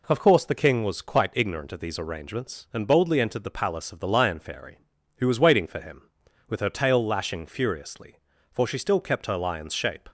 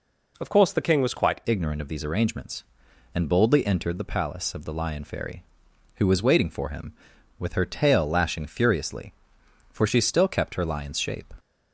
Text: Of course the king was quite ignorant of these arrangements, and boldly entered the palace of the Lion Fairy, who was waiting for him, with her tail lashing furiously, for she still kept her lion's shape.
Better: first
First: none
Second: changes voice at "ignorant"; from 1.4 s on; 9.9 s long

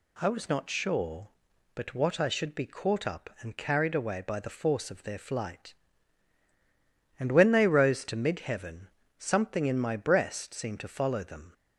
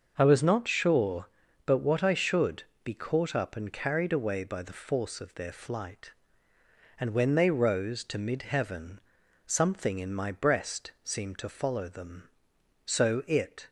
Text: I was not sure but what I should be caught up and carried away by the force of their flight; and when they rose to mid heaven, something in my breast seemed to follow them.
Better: first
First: none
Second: starts louder than the rest; until 1.1 s; 6.5 dB // pauses between "should" and "be"; slight; at 2.6 s; 0.18 s long // goes on to say "So it"; noticeable; from 12.8 s on; 0.84 s long

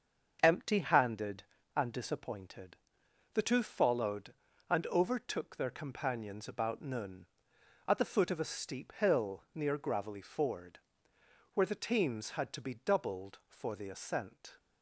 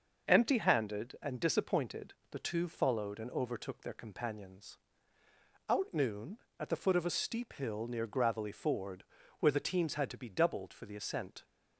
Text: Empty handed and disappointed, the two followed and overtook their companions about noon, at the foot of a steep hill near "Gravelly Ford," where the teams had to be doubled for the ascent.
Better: first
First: starts louder than the rest; until 1.4 s; 7 dB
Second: starts louder than the rest; until 1.3 s; 6 dB // says "out" for "about"; at 5.6 s

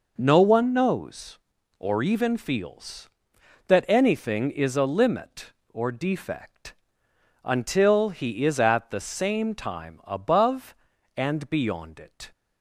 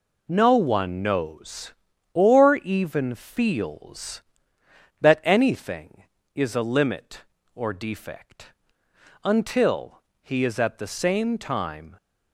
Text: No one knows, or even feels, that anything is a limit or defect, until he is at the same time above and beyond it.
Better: first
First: none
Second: pauses between "until" and "he"; slight; at 10.0 s; 0.20 s long // stops before "above and beyond it"; at 11.9 s

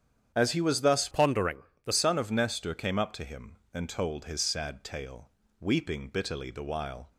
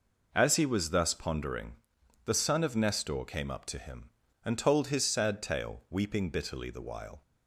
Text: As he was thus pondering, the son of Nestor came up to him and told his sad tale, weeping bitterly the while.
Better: second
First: starts louder than the rest; strong; until 1.3 s; 8.5 dB // changes voice from "pondering" to "the"; from 1.1 to 1.9 s; 0.8 s long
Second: none

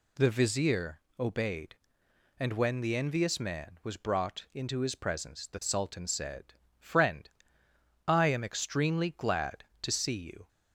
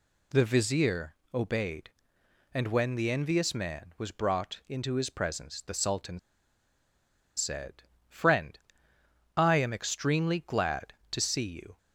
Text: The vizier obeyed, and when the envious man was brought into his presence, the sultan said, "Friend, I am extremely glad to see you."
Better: first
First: pauses between "vizier" and "obeyed"; slight; at 0.9 s; 0.20 s long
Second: pauses between "vizier" and "obeyed"; slight; at 1.1 s; 0.20 s long // pauses between "sultan" and "said"; at 6.1 s; 1.1 s long

